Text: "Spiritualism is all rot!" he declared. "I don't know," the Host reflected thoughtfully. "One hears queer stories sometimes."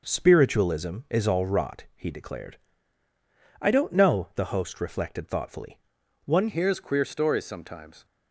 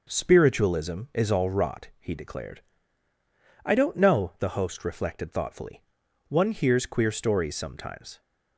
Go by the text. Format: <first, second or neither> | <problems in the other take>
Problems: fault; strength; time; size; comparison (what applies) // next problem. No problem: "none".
second | changes voice at "hears"; from 6.4 s on; 1.6 s long